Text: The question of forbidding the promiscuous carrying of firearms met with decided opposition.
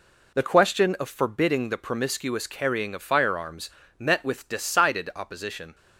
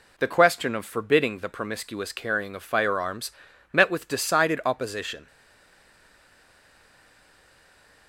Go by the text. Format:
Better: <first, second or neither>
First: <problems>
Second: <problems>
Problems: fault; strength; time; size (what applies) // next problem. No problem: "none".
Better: first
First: pauses between "firearms" and "met"; slight; at 3.7 s; 0.28 s long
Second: pauses between "firearms" and "met"; at 3.3 s; 0.40 s long // stays silent after the last word; strong; from 5.2 s on; 2.8 s long